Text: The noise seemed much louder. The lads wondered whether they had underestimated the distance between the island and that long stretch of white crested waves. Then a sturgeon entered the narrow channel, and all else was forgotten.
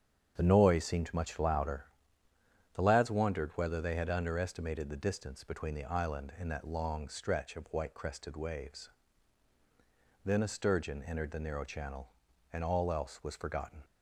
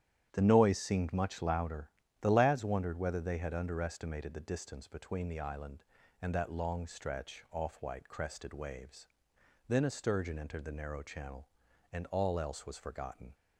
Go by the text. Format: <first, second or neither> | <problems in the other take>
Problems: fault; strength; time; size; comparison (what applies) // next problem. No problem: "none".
first | starts louder than the rest; strong; until 1.3 s; 10.5 dB; strong in the first // says "off" for "of"; at 7.4 s